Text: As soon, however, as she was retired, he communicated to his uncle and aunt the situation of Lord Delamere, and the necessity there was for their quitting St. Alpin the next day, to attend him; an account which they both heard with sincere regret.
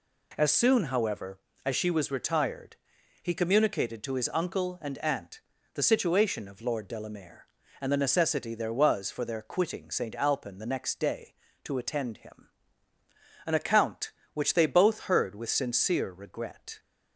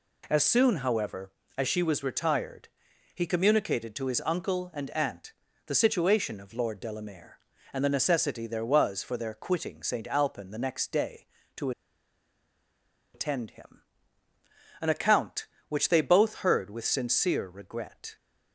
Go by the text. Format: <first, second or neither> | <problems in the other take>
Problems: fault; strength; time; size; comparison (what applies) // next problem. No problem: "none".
first | pauses between "aunt" and "the"; slight; at 5.3 s; 0.34 s long; slight in the first // pauses between "to" and "attend"; strong; at 11.7 s; 1.4 s long